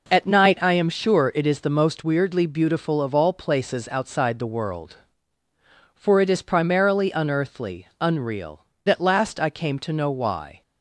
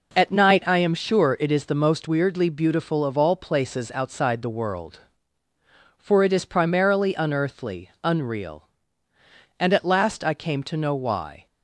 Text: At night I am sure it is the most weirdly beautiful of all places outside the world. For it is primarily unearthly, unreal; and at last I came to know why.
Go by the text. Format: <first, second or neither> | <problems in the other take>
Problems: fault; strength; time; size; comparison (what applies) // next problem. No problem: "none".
second | skips "and"; at 8.7 s